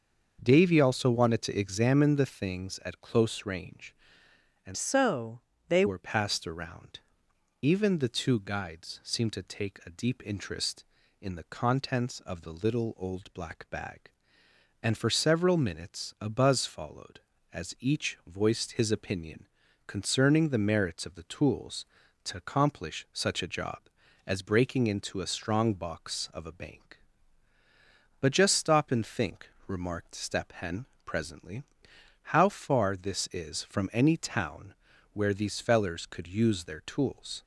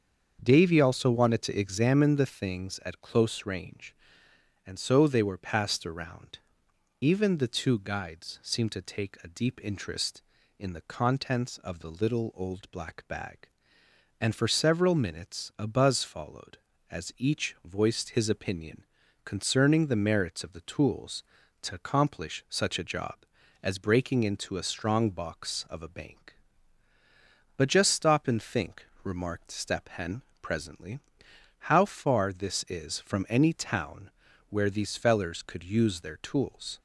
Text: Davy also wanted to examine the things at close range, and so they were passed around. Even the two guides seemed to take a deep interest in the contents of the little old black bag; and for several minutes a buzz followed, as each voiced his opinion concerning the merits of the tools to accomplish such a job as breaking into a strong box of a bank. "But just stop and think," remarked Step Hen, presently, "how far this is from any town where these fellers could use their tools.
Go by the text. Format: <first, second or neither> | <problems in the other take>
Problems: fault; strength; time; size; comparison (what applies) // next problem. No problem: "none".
second | starts louder than the rest; until 1.4 s; 6.5 dB; also in the second // changes voice from "so" to "they"; from 4.7 to 5.8 s; 1.1 s long // pauses between "so" and "they"; slight; at 5.4 s; 0.28 s long // pauses between "opinion" and "concerning"; at 19.4 s; 0.40 s long; also in the second // pauses between "town" and "where"; at 34.7 s; 0.40 s long; also in the second